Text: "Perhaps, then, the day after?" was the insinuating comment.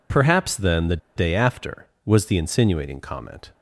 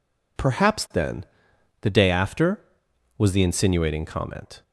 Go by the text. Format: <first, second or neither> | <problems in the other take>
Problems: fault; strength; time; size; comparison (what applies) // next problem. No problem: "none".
second | pauses between "the" and "day"; slight; at 0.9 s; 0.19 s long